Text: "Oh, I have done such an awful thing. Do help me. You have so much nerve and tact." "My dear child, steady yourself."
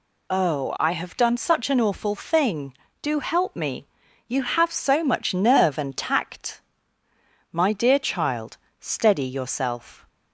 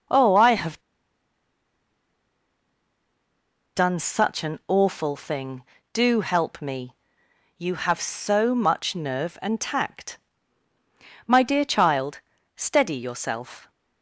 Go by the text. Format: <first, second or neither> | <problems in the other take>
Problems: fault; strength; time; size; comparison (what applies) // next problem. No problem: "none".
first | pauses between "have" and "done"; strong; at 0.7 s; 2.9 s long